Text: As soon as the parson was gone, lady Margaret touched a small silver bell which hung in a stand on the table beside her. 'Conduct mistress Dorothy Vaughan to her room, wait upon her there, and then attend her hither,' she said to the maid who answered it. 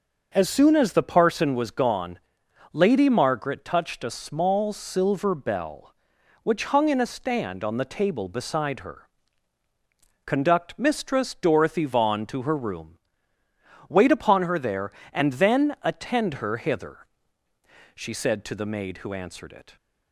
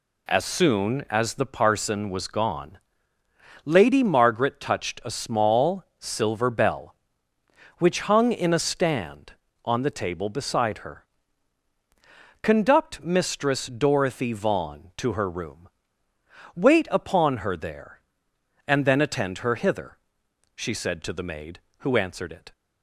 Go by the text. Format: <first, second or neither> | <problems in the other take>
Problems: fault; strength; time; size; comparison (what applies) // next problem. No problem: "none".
neither | none